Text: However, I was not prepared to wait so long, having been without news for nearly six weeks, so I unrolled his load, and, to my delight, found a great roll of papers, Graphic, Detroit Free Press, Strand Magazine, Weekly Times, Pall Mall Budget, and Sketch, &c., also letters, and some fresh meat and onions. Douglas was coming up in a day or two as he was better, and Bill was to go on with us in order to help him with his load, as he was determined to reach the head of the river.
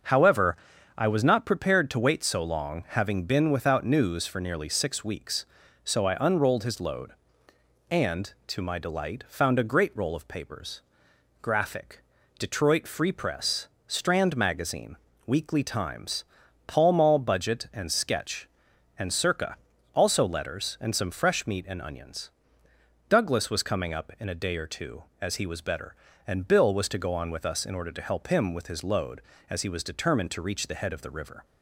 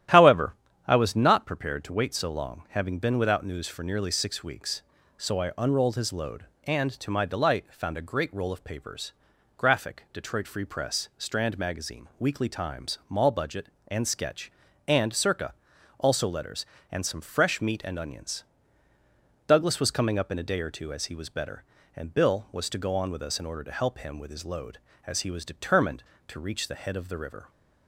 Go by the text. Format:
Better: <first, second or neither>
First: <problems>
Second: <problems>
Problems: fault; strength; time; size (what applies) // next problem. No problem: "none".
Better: first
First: starts louder than the rest; until 1.4 s; 6.5 dB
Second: starts louder than the rest; strong; until 1.4 s; 12 dB // skips "Pall"; at 13.0 s